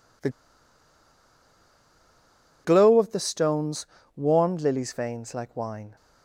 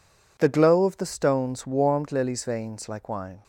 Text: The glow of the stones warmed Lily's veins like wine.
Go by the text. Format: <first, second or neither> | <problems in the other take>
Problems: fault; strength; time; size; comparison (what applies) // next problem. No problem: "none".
second | pauses between "The" and "glow"; strong; at 0.2 s; 2.3 s long // pauses between "stones" and "warmed"; slight; at 3.8 s; 0.30 s long